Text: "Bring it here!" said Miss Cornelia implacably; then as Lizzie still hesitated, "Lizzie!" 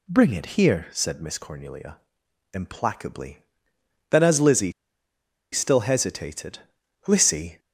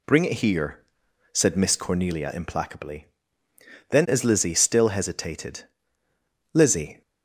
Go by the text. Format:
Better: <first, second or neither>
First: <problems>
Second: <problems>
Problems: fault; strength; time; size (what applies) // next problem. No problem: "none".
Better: second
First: pauses between "Cornelia" and "implacably"; noticeable; at 1.9 s; 0.56 s long // pauses between "Lizzie" and "still"; noticeable; at 4.7 s; 0.80 s long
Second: none